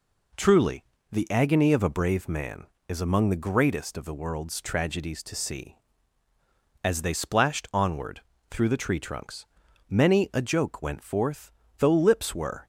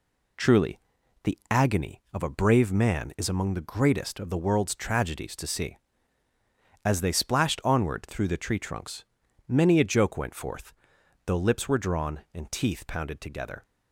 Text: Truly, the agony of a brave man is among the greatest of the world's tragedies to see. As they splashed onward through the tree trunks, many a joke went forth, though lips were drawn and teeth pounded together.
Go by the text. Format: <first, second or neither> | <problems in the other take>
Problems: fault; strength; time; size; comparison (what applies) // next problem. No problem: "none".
second | pauses between "onward" and "through"; slight; at 8.1 s; 0.30 s long // stops before "drawn and teeth pounded together"; at 12.6 s